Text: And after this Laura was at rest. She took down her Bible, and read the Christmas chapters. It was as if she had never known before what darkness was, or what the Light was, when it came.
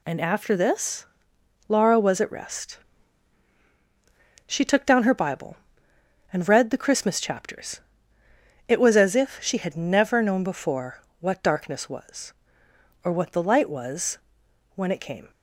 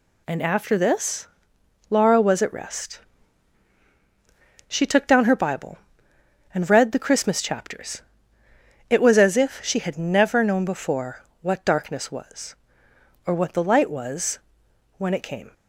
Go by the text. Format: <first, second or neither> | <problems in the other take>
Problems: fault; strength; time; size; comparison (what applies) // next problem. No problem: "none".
neither | pauses between "this" and "Laura"; noticeable; the same in both // pauses between "before" and "what"; slight; the same in both